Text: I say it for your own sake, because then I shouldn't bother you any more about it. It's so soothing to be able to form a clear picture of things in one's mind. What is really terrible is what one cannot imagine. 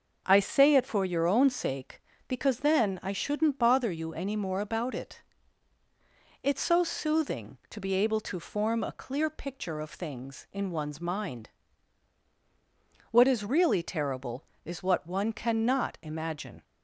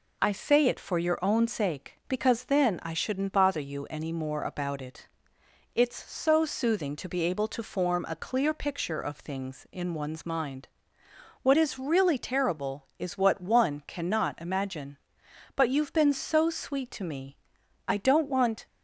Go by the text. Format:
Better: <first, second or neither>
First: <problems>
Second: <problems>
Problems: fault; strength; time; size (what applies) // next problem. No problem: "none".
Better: first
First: none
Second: goes on to say "But you've been so sweet to me I don't want"; strong; from 15.5 s on; 3.1 s long